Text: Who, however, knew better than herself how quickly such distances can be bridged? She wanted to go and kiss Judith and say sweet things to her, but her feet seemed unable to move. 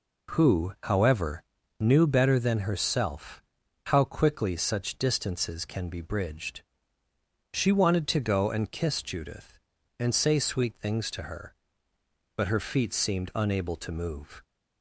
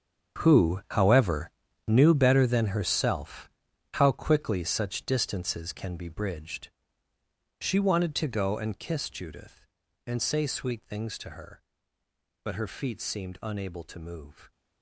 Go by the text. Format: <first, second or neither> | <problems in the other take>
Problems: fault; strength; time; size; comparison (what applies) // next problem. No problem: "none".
first | gets quieter; strong; throughout; 14.5 dB // pauses between "herself" and "how"; noticeable; at 3.4 s; 0.46 s long; noticeable in the first